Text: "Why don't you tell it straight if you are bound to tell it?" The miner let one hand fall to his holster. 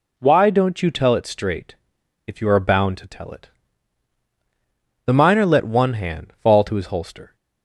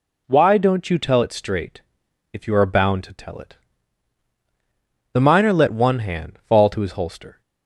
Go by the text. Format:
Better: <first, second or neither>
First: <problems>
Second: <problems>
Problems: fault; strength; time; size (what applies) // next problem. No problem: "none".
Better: neither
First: pauses between "straight" and "if"; noticeable; at 1.7 s; 0.52 s long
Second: pauses between "straight" and "if"; noticeable; at 1.8 s; 0.52 s long